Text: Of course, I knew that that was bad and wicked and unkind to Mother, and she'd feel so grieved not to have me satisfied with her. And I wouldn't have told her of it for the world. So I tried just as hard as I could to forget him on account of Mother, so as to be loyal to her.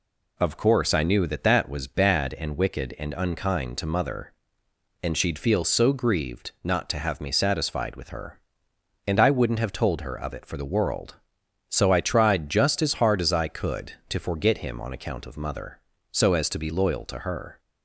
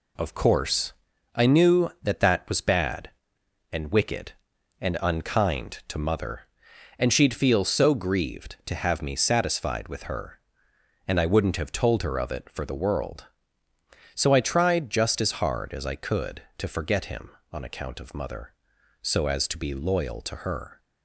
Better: first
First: none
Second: skips "not"; at 8.6 s

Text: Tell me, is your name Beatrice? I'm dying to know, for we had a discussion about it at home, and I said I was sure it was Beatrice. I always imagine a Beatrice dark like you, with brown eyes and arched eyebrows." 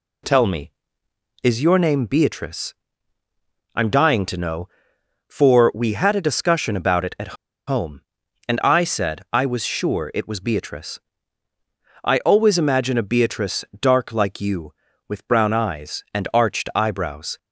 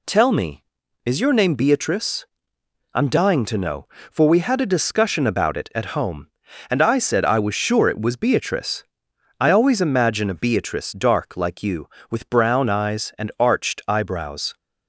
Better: second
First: pauses between "at" and "home"; slight; at 7.3 s; 0.31 s long // pauses between "Beatrice" and "dark"; slight; at 13.6 s; 0.16 s long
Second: none

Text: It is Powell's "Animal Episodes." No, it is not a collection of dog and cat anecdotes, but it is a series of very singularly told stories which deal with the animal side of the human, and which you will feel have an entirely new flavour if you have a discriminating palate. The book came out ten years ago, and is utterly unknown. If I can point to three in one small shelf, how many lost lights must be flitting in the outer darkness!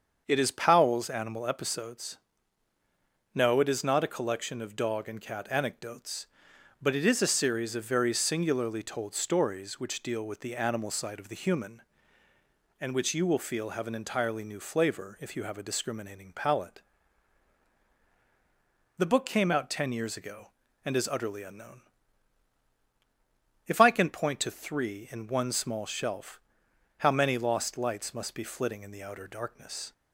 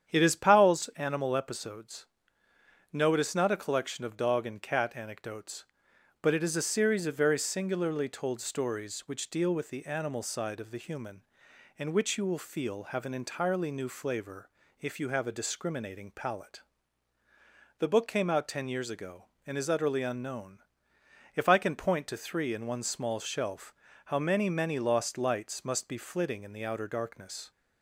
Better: first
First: starts louder than the rest; until 1.2 s; 7 dB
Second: starts louder than the rest; strong; until 1.1 s; 8.5 dB // pauses between "flavour" and "if"; slight; at 14.4 s; 0.30 s long // says "many" twice; at 24.5 s

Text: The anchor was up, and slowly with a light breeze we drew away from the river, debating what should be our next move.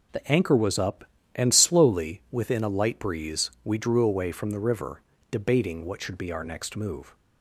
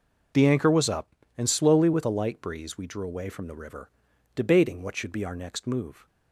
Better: second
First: says "within" for "with"; at 2.3 s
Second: none

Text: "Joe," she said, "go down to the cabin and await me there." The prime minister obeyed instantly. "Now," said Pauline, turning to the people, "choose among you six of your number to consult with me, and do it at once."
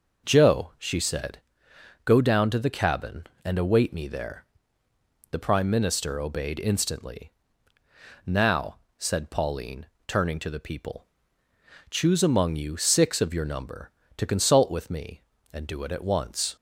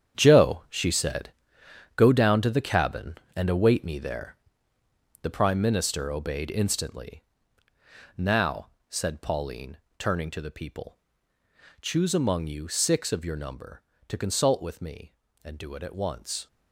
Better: first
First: none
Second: gets quieter; strong; throughout; 11 dB

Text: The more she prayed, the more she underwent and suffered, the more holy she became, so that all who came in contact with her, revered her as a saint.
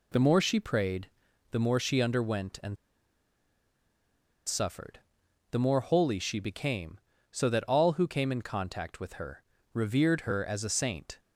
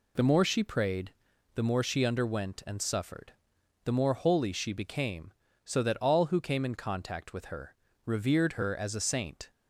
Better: second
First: pauses between "and" and "suffered"; strong; at 2.7 s; 1.7 s long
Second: none

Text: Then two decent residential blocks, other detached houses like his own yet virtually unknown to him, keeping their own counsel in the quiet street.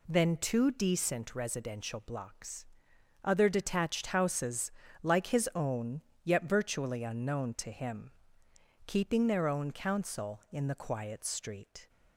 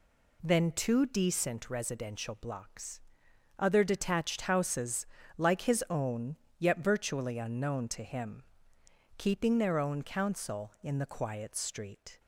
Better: neither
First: pauses between "houses" and "like"; slight; at 4.7 s; 0.32 s long // pauses between "own" and "yet"; slight; at 6.0 s; 0.22 s long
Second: pauses between "houses" and "like"; slight; at 5.0 s; 0.32 s long // pauses between "own" and "yet"; slight; at 6.3 s; 0.22 s long

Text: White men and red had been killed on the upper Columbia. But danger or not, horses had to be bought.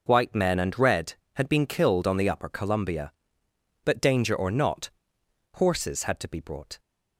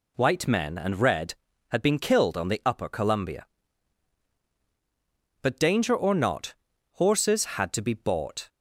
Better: second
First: says "brought" for "bought"; at 6.3 s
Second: none

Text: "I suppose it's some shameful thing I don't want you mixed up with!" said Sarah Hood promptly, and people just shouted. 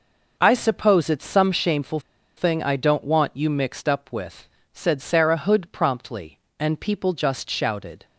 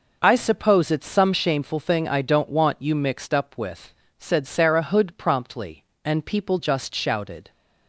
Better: second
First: pauses between "shameful" and "thing"; at 1.9 s; 0.37 s long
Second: none

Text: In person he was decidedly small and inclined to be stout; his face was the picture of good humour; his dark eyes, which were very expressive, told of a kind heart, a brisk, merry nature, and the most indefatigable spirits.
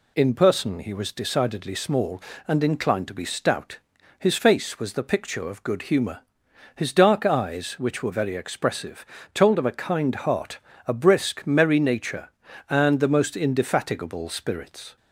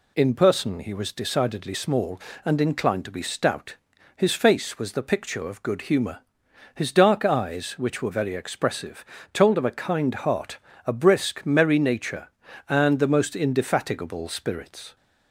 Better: neither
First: none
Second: none

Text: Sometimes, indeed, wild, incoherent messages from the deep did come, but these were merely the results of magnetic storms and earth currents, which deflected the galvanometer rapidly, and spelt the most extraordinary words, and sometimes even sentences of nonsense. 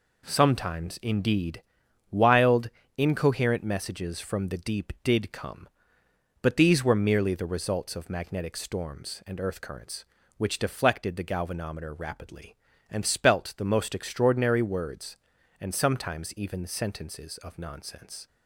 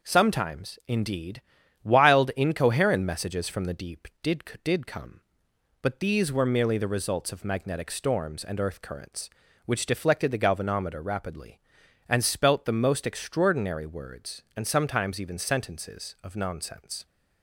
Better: first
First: none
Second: says "did" twice; at 4.6 s

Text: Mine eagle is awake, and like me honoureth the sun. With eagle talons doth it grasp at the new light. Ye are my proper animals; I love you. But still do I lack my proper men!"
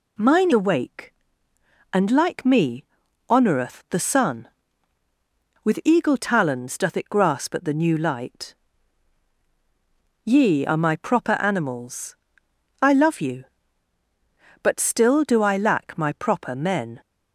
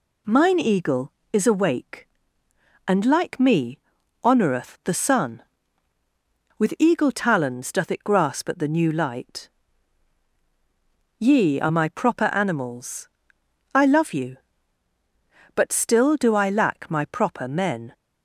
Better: second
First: skips "eagle is"; at 0.5 s // pauses between "me" and "honoureth"; noticeable; at 2.8 s; 0.46 s long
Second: pauses between "me" and "honoureth"; noticeable; at 3.7 s; 0.46 s long

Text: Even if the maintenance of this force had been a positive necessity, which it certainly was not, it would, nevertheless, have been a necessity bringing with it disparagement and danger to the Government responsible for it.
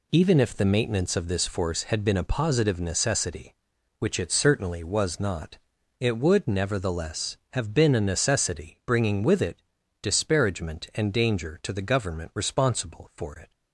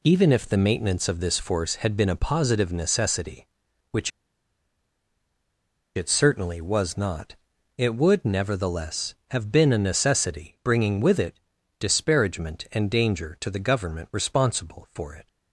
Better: first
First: pauses between "it" and "disparagement"; at 9.6 s; 0.40 s long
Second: pauses between "which" and "it"; strong; at 4.0 s; 1.8 s long // pauses between "it" and "disparagement"; at 11.3 s; 0.40 s long

